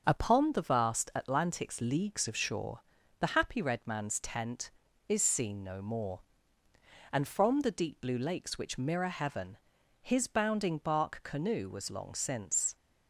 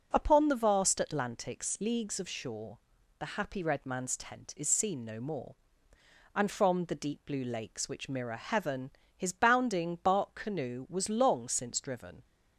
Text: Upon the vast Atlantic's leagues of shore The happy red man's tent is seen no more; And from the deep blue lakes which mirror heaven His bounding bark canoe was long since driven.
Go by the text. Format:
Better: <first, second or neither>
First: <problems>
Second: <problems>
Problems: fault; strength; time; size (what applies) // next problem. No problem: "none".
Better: second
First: starts louder than the rest; noticeable; until 1.0 s; 6 dB // pauses between "shore" and "The"; at 2.8 s; 0.40 s long // pauses between "heaven" and "His"; noticeable; at 9.5 s; 0.46 s long // stops before "driven"; at 12.7 s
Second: pauses between "shore" and "The"; at 2.7 s; 0.38 s long // pauses between "heaven" and "His"; slight; at 8.8 s; 0.26 s long